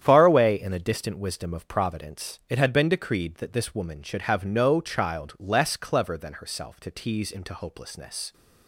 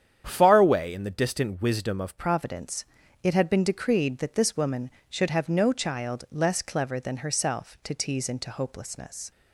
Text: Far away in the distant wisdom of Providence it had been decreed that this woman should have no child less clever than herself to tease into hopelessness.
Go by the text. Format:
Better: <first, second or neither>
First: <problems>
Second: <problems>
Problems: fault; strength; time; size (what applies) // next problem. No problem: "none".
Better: first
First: starts louder than the rest; strong; until 1.0 s; 9.5 dB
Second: starts louder than the rest; strong; until 1.2 s; 9 dB // changes voice at "Providence"; from 2.1 s on; 7.2 s long // pauses between "Providence" and "it"; at 2.8 s; 0.38 s long